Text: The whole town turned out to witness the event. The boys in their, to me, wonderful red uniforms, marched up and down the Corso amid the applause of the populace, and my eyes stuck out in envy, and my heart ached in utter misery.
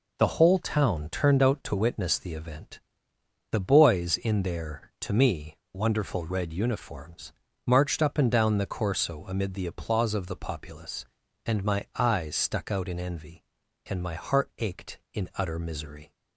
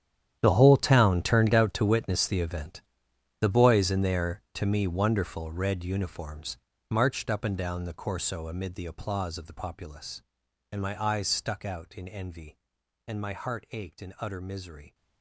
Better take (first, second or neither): first